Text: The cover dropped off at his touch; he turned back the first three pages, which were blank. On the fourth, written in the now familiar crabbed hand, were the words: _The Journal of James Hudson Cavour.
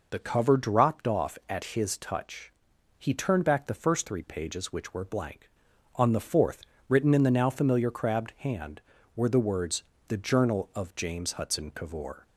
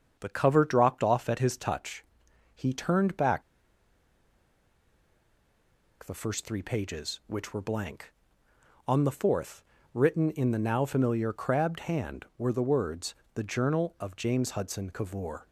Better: first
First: none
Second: starts louder than the rest; strong; until 1.2 s; 7.5 dB // pauses between "back" and "the"; strong; at 3.4 s; 2.6 s long

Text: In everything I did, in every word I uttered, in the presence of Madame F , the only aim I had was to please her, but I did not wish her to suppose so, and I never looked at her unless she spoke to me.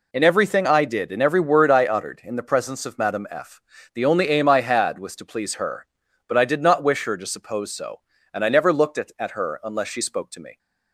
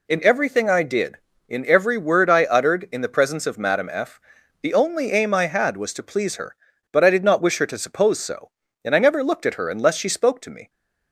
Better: second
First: says "at" twice; at 9.1 s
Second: none

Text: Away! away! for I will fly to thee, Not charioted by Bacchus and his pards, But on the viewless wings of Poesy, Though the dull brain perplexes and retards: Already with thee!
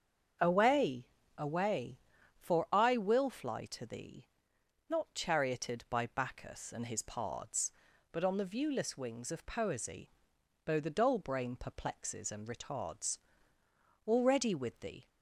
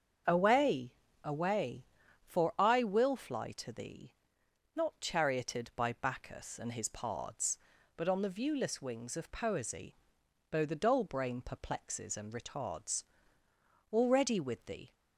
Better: neither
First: starts louder than the rest; until 1.7 s; 7 dB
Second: starts louder than the rest; until 1.6 s; 7 dB

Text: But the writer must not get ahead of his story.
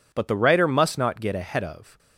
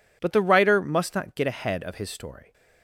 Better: second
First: stops before "his story"; at 1.9 s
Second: none

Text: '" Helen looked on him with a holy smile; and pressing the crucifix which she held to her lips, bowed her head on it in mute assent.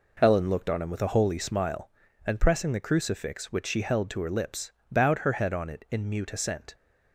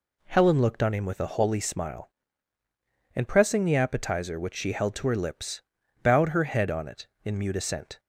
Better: first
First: none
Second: says "appetizer" for "crucifix"; at 3.7 s

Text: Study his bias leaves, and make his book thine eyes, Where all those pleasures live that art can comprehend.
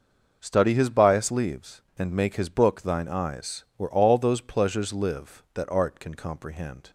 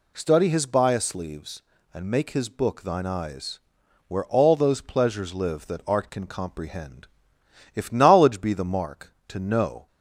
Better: first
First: none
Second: goes on to say "If knowledge be the mark to know"; strong; from 7.7 s on; 2.1 s long

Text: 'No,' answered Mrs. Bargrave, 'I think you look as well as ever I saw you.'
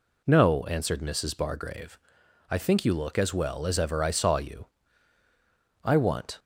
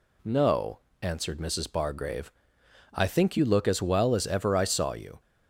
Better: second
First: goes on to say "I want"; from 5.8 s on; 0.56 s long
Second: none

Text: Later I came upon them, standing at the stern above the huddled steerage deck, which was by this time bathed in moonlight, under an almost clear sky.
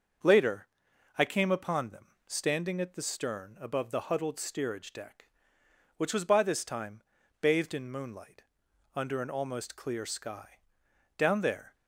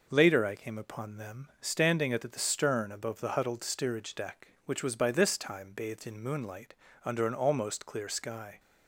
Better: second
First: starts louder than the rest; until 1.7 s; 6.5 dB // pauses between "Later" and "I"; noticeable; at 0.6 s; 0.50 s long // pauses between "time" and "bathed"; at 7.0 s; 0.40 s long // goes on to say "Down there"; from 11.1 s on; 0.58 s long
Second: none

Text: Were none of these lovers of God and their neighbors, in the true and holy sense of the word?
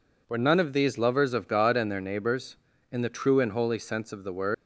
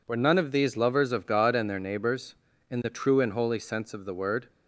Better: second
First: leaves "word" unfinished; at 4.5 s; 130 ms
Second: none

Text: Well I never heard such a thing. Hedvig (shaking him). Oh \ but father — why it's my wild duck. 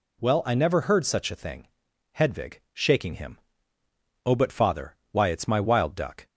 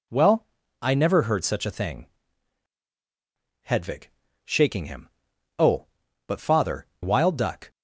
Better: first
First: none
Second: pauses between "Well" and "I"; slight; at 0.4 s; 0.34 s long // skips "why it's my"; at 6.9 s

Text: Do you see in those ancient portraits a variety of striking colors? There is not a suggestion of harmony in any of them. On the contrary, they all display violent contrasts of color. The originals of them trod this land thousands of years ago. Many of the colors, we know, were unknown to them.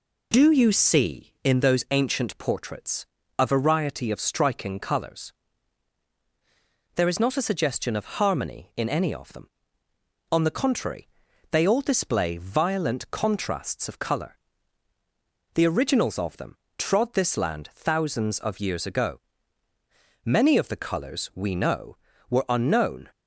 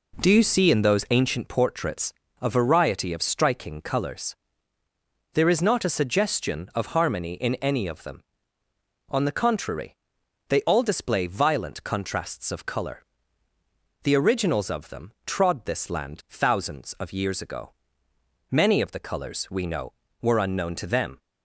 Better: second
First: pauses between "portraits" and "a"; slight; at 3.0 s; 0.34 s long // pauses between "them" and "trod"; slight; at 16.5 s; 0.22 s long // stops before "to them"; at 23.1 s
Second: pauses between "portraits" and "a"; slight; at 2.1 s; 0.28 s long // pauses between "them" and "trod"; slight; at 15.1 s; 0.16 s long

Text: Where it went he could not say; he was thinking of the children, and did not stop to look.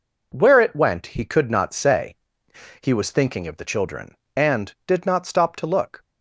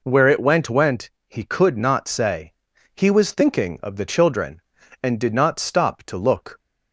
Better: first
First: none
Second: says "went" twice; at 0.6 s

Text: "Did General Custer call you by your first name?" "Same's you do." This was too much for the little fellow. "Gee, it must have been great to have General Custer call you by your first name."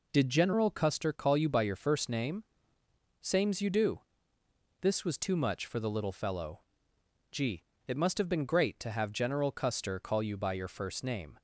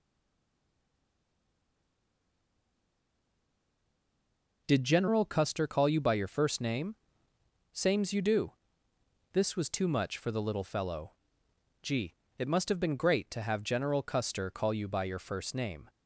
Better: first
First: none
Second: stays silent before the first word; strong; until 4.6 s; 4.6 s long

